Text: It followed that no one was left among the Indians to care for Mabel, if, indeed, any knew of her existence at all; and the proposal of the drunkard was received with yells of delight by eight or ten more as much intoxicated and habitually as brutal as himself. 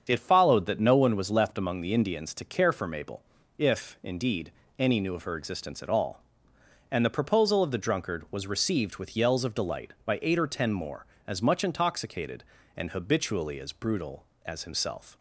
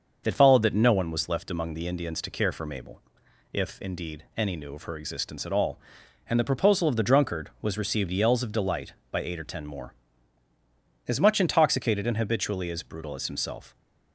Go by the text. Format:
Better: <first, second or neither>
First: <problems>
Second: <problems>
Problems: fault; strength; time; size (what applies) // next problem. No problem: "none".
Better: first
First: starts louder than the rest; strong; until 1.0 s; 7 dB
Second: starts louder than the rest; until 1.2 s; 6 dB // skips "with"; at 8.1 s